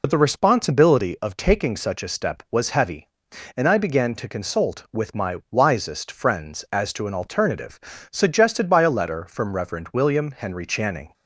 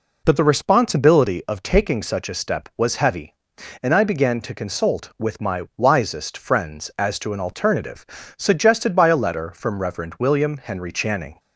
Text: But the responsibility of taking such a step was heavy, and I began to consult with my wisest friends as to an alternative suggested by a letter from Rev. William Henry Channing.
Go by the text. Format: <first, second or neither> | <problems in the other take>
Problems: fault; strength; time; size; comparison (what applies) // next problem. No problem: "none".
second | loses the start of "But"; at 0.0 s; 55 ms // pauses between "alternative" and "suggested"; slight; at 7.7 s; 0.34 s long; slight in the second